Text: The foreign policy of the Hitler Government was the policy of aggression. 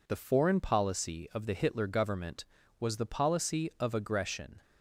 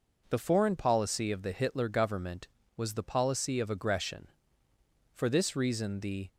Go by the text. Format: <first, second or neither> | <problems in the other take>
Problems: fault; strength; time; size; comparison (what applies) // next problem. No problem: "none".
first | goes on to say "For this reason the"; noticeable; from 5.1 s on; 1.1 s long